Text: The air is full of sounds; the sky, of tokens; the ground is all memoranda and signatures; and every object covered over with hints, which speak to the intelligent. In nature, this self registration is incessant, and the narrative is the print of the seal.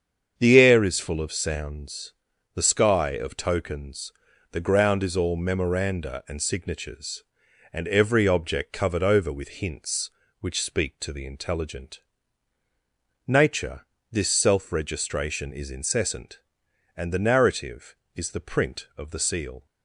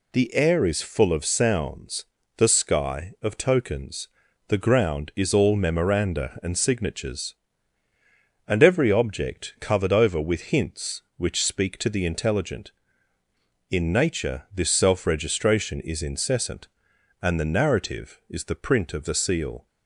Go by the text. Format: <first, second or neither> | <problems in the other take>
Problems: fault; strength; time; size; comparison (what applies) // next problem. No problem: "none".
second | starts louder than the rest; strong; until 1.3 s; 7.5 dB // skips "In"; at 12.6 s